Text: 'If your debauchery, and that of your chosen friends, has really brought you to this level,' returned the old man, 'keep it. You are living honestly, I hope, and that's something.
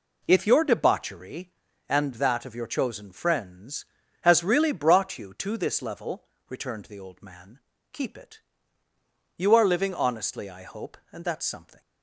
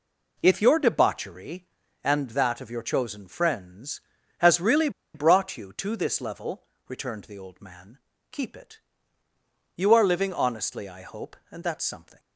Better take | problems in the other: first | pauses between "really" and "brought"; slight; at 4.8 s; 0.25 s long

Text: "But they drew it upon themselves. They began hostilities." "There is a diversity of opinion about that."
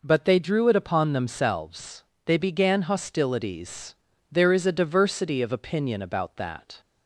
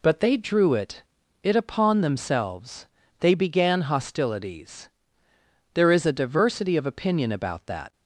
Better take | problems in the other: first | says "it" twice; at 1.4 s

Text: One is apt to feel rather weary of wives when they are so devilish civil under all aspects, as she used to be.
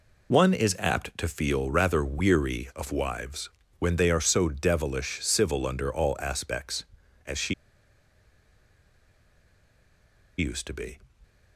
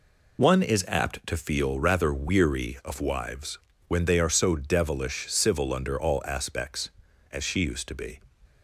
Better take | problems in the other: second | pauses between "wives" and "when"; slight; at 3.4 s; 0.30 s long; slight in the second // pauses between "she" and "used"; strong; at 7.5 s; 2.8 s long

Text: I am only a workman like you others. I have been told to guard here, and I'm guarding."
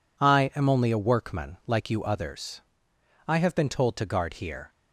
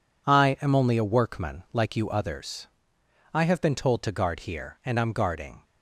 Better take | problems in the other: second | stops before "and I'm guarding"; at 4.7 s

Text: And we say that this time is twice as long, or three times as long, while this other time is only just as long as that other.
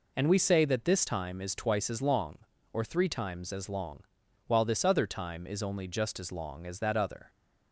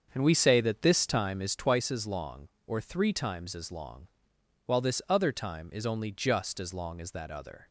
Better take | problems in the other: first | starts louder than the rest; until 1.6 s; 7 dB

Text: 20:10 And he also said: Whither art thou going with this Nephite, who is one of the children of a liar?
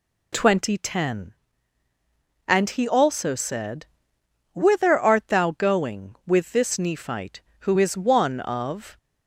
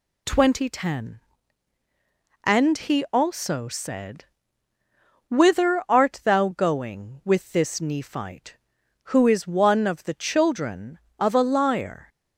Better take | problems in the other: second | stops before "the children of a liar"; at 8.9 s

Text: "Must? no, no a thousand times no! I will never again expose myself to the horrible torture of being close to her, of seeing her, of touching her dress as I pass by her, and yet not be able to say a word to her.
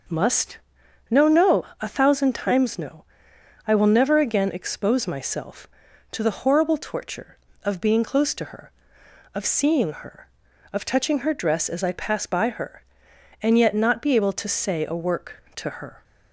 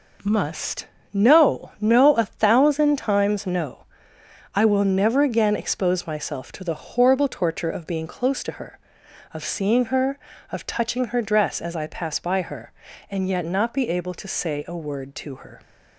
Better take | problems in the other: second | pauses between "no" and "a"; slight; at 1.6 s; 0.16 s long // says "work" for "word"; at 14.9 s

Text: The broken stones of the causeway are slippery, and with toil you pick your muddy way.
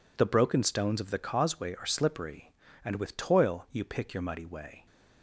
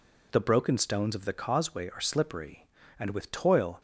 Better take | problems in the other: first | stops before "you pick your muddy way"; at 3.7 s

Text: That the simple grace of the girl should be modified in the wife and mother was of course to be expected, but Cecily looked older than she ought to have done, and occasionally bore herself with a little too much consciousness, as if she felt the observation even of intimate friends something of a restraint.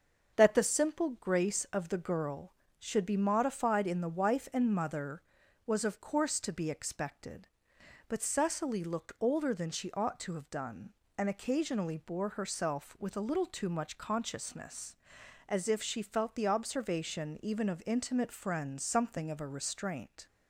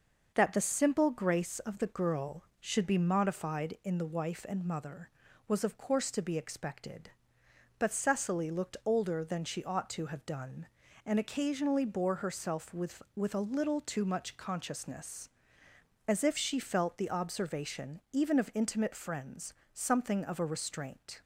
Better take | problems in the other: first | starts louder than the rest; until 1.3 s; 6 dB; also in the first // says "with" twice; at 13.1 s // pauses between "friends" and "something"; slight; at 19.5 s; 0.22 s long

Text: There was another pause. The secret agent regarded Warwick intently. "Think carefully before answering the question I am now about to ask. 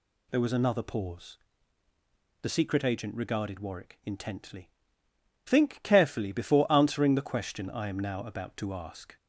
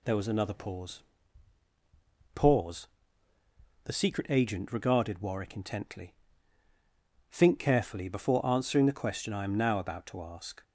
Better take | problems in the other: first | says "pause" twice; at 2.3 s

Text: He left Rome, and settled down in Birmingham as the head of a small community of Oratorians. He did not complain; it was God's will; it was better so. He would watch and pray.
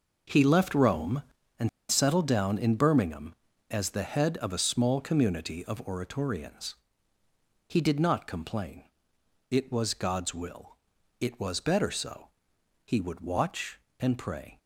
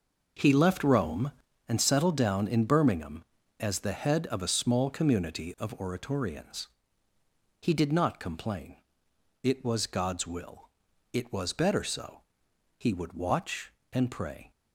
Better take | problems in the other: second | pauses between "and" and "settled"; slight; at 1.6 s; 0.22 s long

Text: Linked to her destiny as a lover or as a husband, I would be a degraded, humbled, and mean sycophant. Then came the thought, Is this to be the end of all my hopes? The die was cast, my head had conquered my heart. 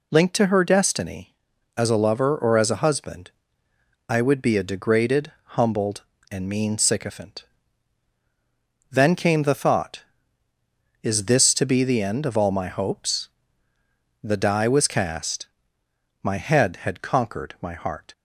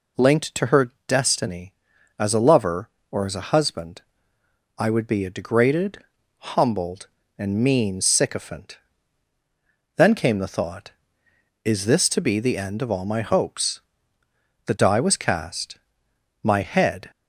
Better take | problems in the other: first | pauses between "her" and "destiny"; slight; at 0.9 s; 0.18 s long // stops before "had conquered my heart"; at 17.1 s

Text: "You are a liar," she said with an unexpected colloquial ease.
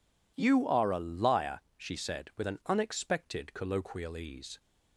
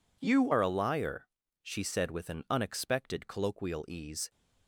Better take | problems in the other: first | changes voice at "are"; from 0.5 s on; 3.8 s long

